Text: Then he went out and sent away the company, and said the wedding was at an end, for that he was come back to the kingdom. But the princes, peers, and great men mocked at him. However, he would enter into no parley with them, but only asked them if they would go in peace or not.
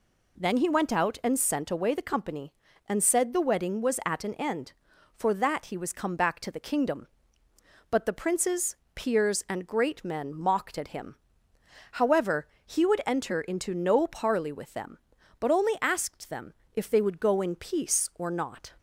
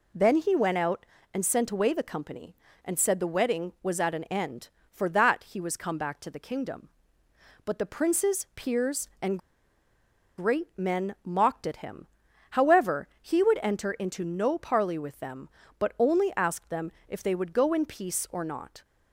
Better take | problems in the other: first | pauses between "and" and "great"; at 9.3 s; 0.99 s long // pauses between "them" and "if"; slight; at 16.9 s; 0.16 s long; slight in the first

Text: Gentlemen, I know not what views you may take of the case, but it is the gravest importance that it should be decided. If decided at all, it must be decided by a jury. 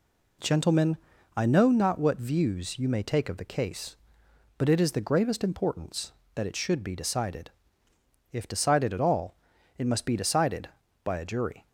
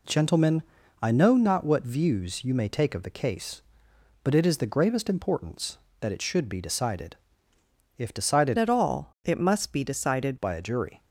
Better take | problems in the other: first | changes voice from "at" to "decided"; from 8.5 to 10.3 s; 1.8 s long

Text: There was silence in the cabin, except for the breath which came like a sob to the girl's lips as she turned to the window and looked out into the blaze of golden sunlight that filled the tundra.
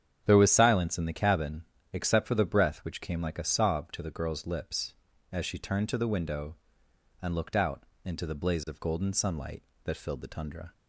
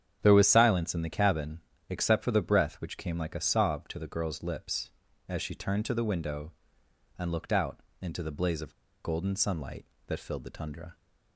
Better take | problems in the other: first | starts louder than the rest; strong; until 1.2 s; 9 dB; strong in the first // pauses between "out" and "into"; slight; at 7.7 s; 0.22 s long; slight in the first // pauses between "of" and "golden"; slight; at 8.7 s; 0.30 s long

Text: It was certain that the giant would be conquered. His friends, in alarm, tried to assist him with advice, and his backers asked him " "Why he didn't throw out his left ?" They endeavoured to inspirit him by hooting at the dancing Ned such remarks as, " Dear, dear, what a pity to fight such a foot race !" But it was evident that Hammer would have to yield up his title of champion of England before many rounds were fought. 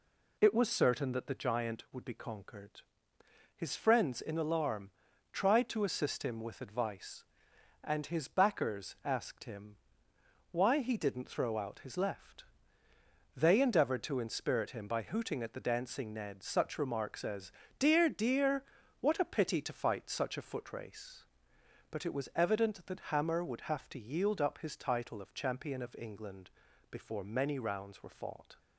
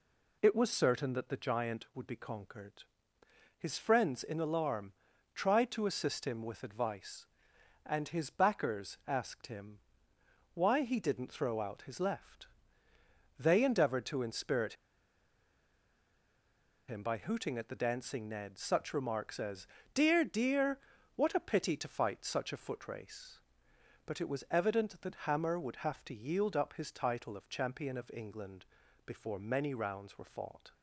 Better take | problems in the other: first | pauses between "inspirit" and "him"; strong; at 14.7 s; 2.1 s long // pauses between "England" and "before"; at 28.6 s; 0.40 s long; also in the first

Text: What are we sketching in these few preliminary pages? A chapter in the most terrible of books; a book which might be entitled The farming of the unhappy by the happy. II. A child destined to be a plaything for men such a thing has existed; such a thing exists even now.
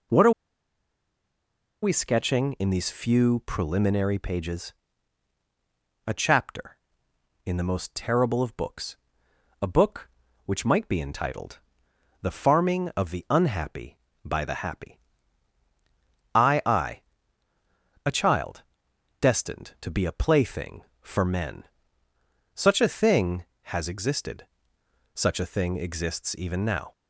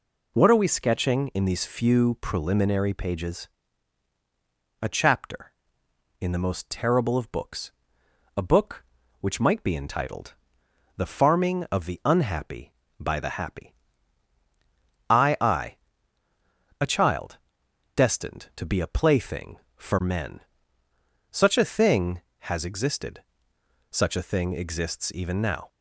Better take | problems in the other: second | pauses between "are" and "we"; strong; at 0.3 s; 1.5 s long // pauses between "entitled" and "The"; noticeable; at 11.5 s; 0.64 s long; noticeable in the second // pauses between "child" and "destined"; noticeable; at 18.6 s; 0.58 s long; noticeable in the second // pauses between "men" and "such"; noticeable; at 21.6 s; 0.90 s long; noticeable in the second

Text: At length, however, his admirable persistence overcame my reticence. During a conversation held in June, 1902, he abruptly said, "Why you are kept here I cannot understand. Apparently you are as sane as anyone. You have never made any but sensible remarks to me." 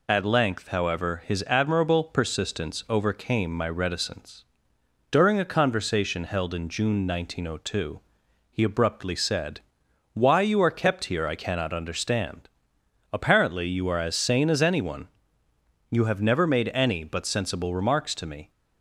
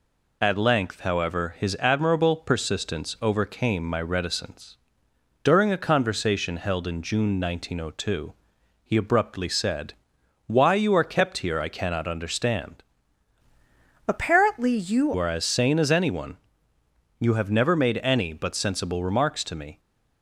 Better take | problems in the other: first | changes voice from "Apparently" to "you"; from 14.0 to 15.1 s; 1.1 s long

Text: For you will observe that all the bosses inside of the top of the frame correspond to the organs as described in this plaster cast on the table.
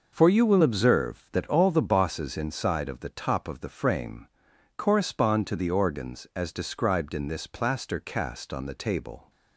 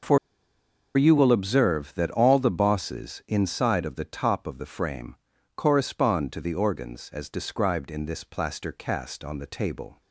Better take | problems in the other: first | pauses between "For" and "you"; noticeable; at 0.1 s; 0.78 s long // pauses between "frame" and "correspond"; at 5.1 s; 0.40 s long; noticeable in the first

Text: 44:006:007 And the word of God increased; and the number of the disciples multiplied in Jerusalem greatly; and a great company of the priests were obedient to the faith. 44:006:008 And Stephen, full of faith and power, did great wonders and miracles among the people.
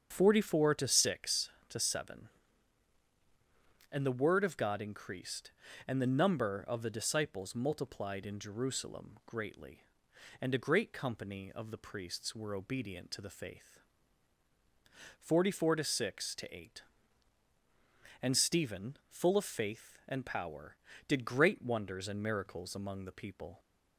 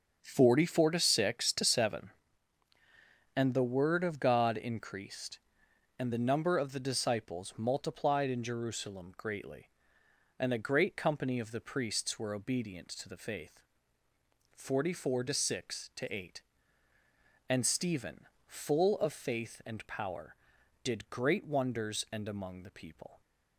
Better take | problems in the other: first | starts louder than the rest; until 1.2 s; 6.5 dB; strong in the first // skips "miracles"; at 22.2 s

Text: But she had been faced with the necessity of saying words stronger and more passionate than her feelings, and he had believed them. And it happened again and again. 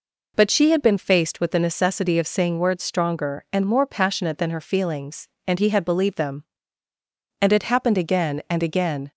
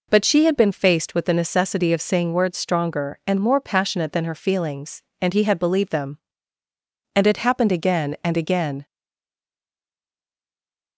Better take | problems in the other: first | stays silent after the last word; from 8.8 s on; 2.1 s long

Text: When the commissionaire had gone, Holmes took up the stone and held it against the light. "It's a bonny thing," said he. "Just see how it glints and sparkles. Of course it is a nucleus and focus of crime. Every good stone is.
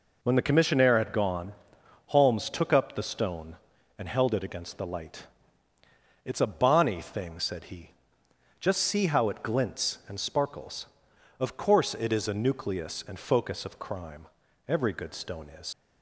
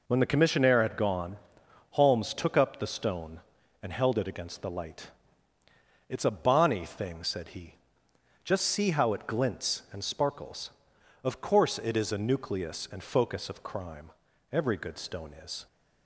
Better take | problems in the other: second | leaves "is" unfinished; at 15.7 s; 95 ms

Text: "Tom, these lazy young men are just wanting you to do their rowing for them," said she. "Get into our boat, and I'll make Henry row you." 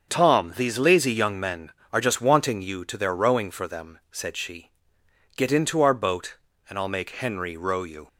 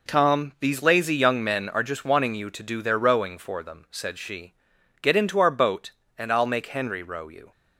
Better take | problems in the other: second | starts louder than the rest; until 1.1 s; 7 dB // skips "do"; at 2.9 s

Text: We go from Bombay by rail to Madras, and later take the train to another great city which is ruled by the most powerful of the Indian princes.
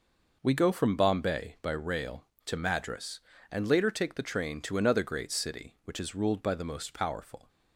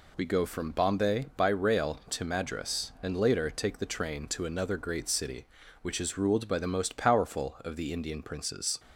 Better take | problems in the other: second | stops before "of the Indian princes"; at 7.4 s

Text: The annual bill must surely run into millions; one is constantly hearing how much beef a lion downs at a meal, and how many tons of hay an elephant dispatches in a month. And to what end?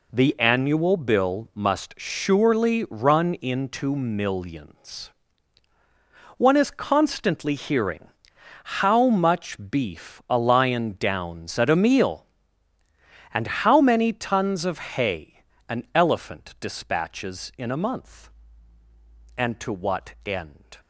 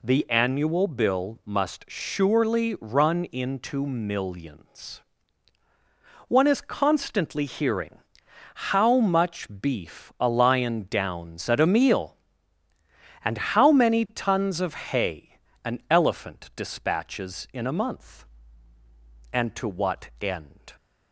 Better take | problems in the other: second | gets quieter; strong; throughout; 9 dB // pauses between "hearing" and "how"; noticeable; at 8.0 s; 0.72 s long; noticeable in the second // pauses between "hay" and "an"; slight; at 15.3 s; 0.28 s long; slight in the second

